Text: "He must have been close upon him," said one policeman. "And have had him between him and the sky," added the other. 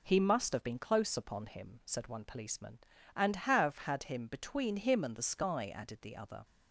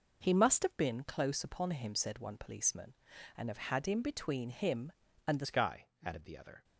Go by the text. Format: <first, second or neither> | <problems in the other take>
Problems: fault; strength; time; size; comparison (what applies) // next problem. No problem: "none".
first | changes voice at "sky"; from 5.4 s on; 1.2 s long